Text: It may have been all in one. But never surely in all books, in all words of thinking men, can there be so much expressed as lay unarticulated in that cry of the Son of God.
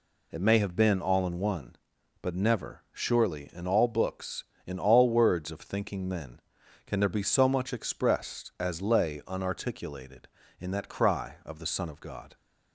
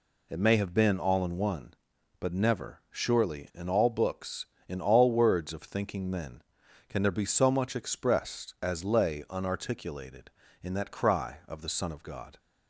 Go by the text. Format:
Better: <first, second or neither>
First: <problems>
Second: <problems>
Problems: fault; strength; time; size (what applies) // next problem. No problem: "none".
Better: neither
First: none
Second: none